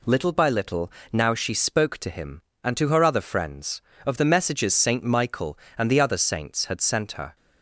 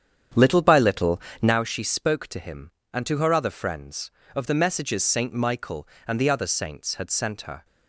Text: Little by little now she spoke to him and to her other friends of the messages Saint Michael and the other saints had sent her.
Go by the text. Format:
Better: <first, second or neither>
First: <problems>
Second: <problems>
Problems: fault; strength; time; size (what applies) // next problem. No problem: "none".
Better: first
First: pauses between "little" and "now"; slight; at 0.9 s; 0.22 s long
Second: starts louder than the rest; strong; until 1.6 s; 8.5 dB // pauses between "little" and "now"; slight; at 1.2 s; 0.22 s long